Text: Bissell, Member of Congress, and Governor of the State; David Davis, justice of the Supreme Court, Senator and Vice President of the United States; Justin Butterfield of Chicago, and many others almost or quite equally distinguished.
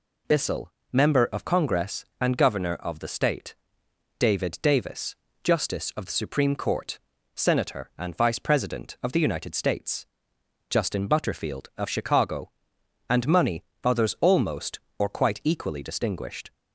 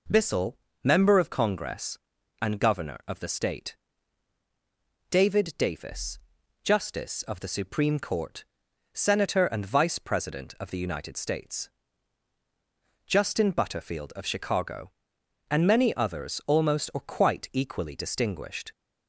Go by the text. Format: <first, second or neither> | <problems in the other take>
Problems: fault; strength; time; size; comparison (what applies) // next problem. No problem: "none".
second | says "money" for "many"; at 13.2 s